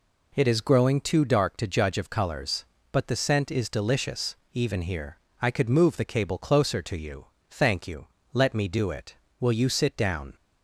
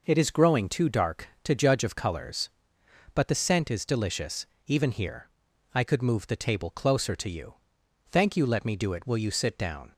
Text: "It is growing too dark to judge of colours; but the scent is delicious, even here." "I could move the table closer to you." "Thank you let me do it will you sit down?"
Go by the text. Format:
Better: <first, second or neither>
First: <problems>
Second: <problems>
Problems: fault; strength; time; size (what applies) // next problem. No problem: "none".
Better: second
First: says "cable" for "table"; at 6.0 s // pauses between "you" and "let"; slight; at 8.0 s; 0.26 s long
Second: none